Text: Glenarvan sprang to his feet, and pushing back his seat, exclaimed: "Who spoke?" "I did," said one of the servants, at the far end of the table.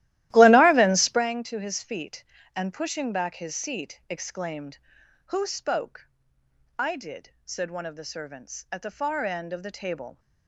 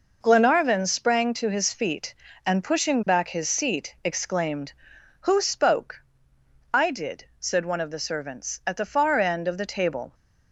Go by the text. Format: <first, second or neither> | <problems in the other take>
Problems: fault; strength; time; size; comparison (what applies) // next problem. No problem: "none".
second | starts louder than the rest; strong; until 1.3 s; 15 dB